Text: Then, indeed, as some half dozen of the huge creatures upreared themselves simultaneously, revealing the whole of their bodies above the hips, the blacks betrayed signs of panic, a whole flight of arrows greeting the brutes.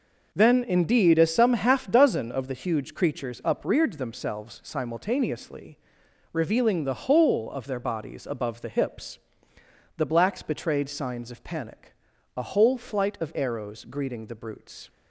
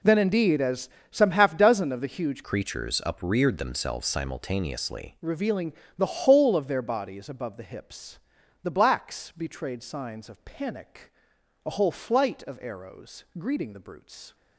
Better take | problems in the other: first | pauses between "as" and "some"; slight; at 0.8 s; 0.22 s long // changes voice from "creatures" to "simultaneously"; from 2.4 to 5.1 s; 2.7 s long // pauses between "revealing" and "the"; slight; at 5.7 s; 0.24 s long

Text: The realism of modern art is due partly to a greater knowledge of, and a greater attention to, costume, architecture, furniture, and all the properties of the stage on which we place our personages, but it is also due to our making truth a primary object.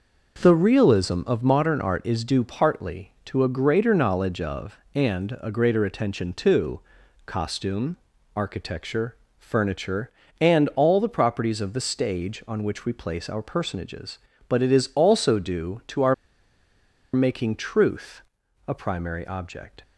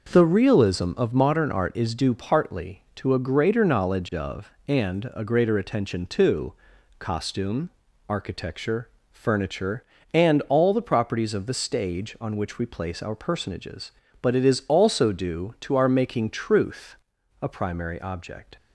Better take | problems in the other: second | pauses between "our" and "making"; at 16.1 s; 0.99 s long // pauses between "truth" and "a"; at 18.2 s; 0.44 s long; also in the second

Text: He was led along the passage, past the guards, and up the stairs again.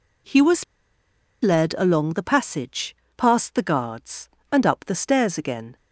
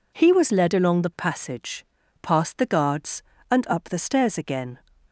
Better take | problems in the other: second | pauses between "was" and "led"; noticeable; at 0.6 s; 0.79 s long

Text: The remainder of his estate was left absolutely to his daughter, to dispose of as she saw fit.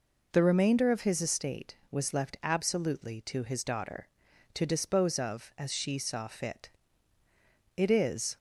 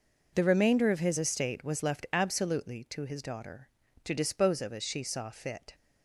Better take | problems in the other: second | goes on to say "It is"; from 7.7 s on; 0.60 s long

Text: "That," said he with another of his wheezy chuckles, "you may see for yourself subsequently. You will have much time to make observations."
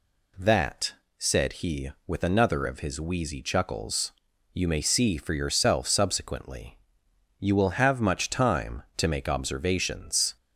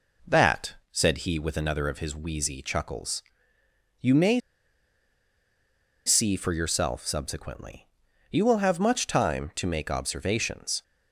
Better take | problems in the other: first | pauses between "may" and "see"; strong; at 4.3 s; 1.6 s long

